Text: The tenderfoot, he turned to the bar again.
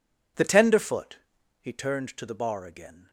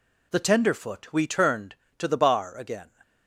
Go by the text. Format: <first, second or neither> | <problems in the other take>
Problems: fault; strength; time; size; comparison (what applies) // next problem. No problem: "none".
first | says "we" for "he"; at 1.1 s